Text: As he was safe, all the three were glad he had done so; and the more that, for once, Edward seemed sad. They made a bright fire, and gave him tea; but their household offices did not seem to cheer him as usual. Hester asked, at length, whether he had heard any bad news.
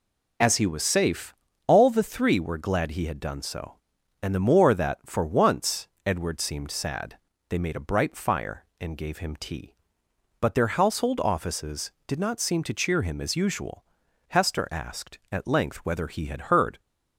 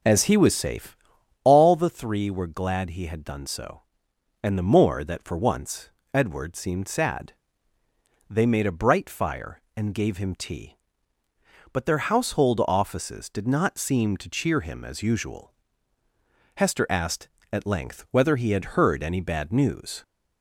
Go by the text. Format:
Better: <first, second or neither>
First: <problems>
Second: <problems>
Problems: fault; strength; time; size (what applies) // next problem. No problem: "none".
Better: second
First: stops before "any bad news"; at 16.7 s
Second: none